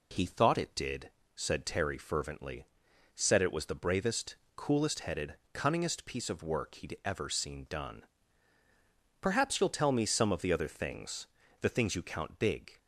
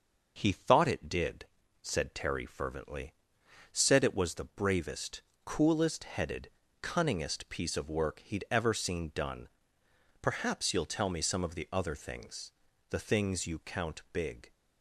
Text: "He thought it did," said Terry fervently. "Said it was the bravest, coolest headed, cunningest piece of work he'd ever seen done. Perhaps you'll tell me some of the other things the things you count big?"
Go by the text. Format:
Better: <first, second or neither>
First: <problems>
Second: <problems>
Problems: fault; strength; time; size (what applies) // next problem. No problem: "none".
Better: neither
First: pauses between "things" and "the"; slight; at 11.2 s; 0.34 s long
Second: pauses between "things" and "the"; at 12.5 s; 0.40 s long